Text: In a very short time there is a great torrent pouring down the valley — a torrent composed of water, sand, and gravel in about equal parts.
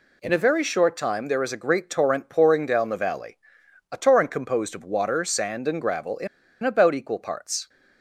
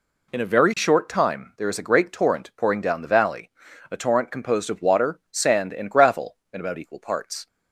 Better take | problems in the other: second | pauses between "in" and "about"; slight; at 6.2 s; 0.35 s long

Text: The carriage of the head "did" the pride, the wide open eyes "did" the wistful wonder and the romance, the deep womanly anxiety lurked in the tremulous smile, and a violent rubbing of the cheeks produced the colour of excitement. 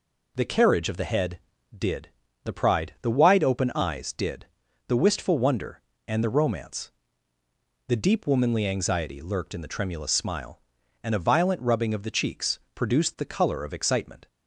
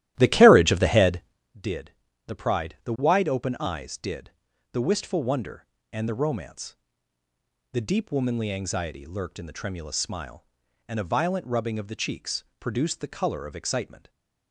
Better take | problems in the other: first | starts louder than the rest; strong; until 1.4 s; 14 dB // pauses between "did" and "the"; slight; at 1.9 s; 0.34 s long; slight in the first // pauses between "did" and "the"; at 4.3 s; 0.40 s long; also in the first // pauses between "cheeks" and "produced"; slight; at 12.4 s; 0.16 s long; slight in the first

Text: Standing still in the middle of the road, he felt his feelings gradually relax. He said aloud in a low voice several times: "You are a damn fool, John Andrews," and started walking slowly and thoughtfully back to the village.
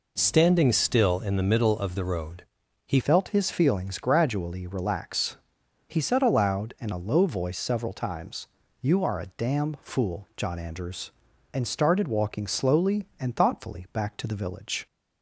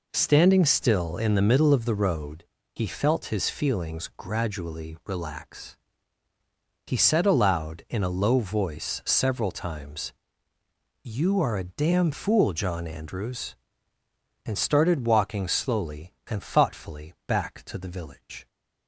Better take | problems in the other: second | changes voice at "felt"; from 3.0 s on; 11.8 s long

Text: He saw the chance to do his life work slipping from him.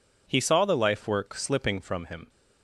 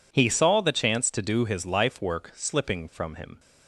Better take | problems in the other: second | skips "chance to do his"; at 0.7 s

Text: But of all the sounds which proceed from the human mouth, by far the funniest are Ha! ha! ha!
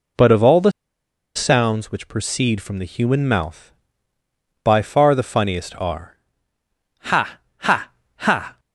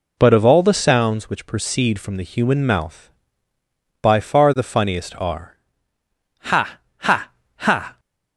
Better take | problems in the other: second | pauses between "the" and "sounds"; noticeable; at 0.7 s; 0.64 s long // pauses between "are" and "Ha"; noticeable; at 6.1 s; 0.84 s long; noticeable in the second

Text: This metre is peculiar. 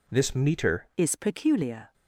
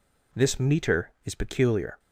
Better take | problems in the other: second | changes voice at "is"; from 0.9 s on; 1.0 s long

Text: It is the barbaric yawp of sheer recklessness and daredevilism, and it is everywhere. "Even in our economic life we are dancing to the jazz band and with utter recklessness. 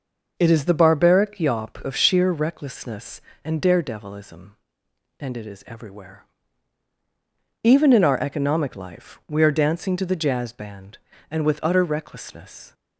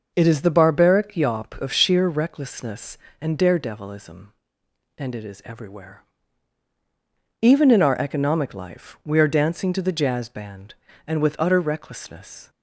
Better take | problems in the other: neither | none

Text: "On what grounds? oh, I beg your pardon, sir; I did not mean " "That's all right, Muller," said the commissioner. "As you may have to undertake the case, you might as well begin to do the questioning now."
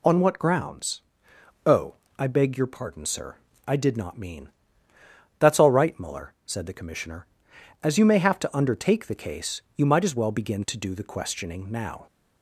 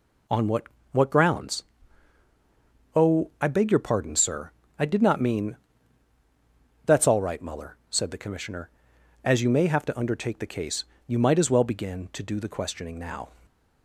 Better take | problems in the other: first | says "what" twice; at 0.9 s

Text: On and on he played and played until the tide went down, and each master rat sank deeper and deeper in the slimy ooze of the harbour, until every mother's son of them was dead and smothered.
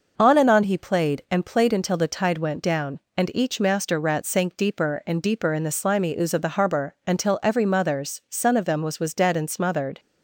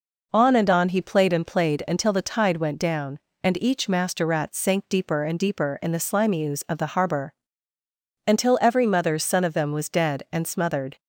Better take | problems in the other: second | says "was" twice; at 8.9 s

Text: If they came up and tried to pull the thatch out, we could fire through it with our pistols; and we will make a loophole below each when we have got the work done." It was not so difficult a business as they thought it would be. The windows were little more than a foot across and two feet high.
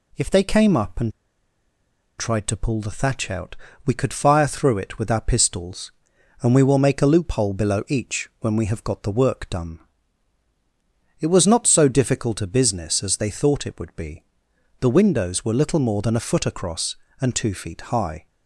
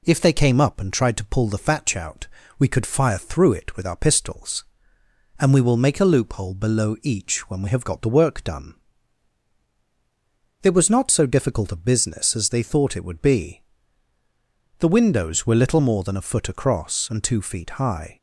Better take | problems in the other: second | pauses between "and" and "tried"; at 1.1 s; 1.0 s long

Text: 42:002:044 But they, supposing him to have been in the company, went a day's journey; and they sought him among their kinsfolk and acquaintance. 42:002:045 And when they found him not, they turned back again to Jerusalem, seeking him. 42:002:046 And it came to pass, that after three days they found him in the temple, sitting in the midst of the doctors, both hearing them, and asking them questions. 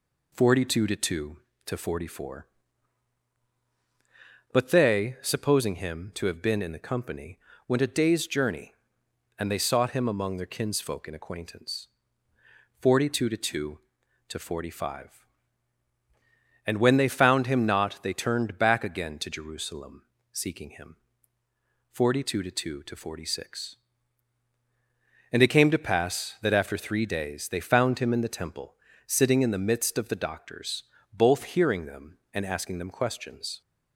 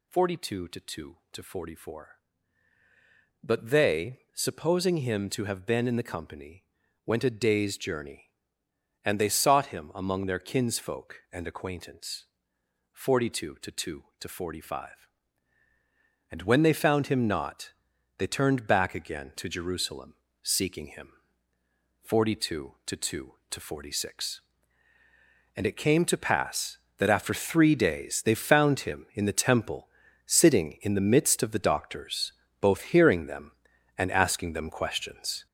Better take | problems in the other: first | gets louder; throughout; 7 dB

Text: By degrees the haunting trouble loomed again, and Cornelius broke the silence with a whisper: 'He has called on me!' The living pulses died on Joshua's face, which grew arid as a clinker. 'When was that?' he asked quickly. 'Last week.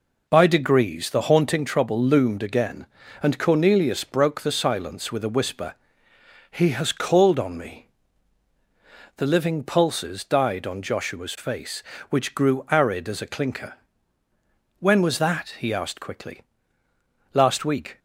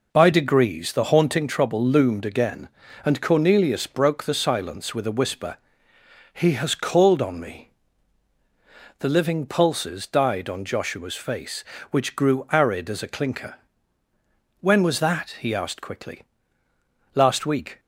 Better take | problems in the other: neither | none

